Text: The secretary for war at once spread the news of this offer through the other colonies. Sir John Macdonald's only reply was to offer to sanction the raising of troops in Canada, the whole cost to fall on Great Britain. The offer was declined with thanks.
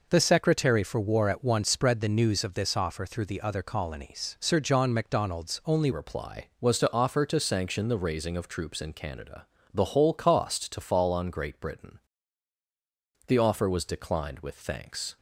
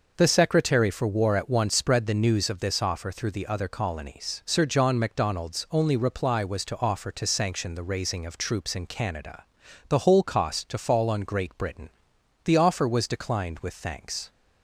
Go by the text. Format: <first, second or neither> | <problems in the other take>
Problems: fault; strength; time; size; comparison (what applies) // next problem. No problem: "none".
second | changes voice at "reply"; from 5.9 s on; 9.2 s long